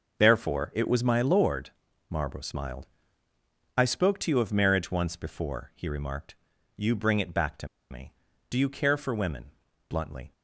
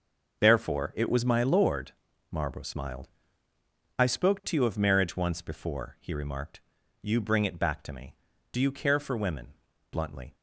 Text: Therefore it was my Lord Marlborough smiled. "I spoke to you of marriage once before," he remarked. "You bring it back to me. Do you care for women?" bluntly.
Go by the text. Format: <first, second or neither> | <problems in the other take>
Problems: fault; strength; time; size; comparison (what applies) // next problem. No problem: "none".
second | pauses between "Lord" and "Marlborough"; at 1.6 s; 0.40 s long; also in the second // pauses between "to" and "me"; slight; at 7.6 s; 0.23 s long